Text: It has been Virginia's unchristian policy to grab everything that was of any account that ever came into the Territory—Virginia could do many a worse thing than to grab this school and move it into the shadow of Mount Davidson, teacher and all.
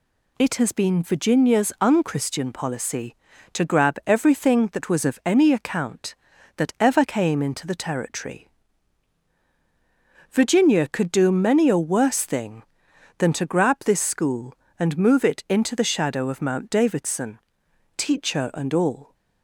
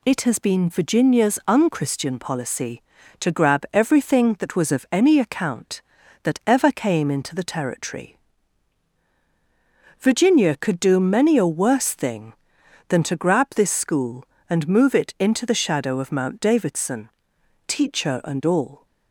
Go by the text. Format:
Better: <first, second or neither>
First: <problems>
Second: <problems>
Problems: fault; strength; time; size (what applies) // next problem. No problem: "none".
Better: neither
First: none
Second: none